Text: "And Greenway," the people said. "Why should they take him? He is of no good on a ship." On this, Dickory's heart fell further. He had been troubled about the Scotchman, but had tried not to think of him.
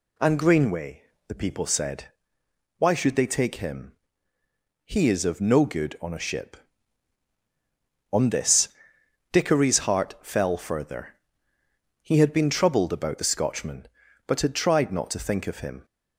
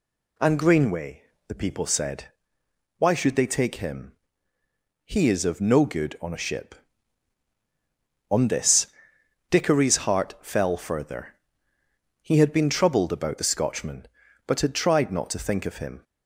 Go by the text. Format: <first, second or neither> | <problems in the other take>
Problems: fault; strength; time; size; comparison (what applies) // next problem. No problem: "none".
neither | none